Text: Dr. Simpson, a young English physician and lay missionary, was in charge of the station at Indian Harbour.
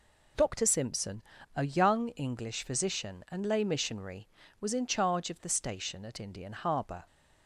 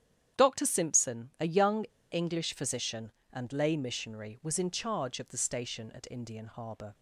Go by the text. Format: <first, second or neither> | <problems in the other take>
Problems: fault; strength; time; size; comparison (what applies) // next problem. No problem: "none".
first | starts louder than the rest; strong; until 1.4 s; 9.5 dB // pauses between "young" and "English"; slight; at 1.8 s; 0.28 s long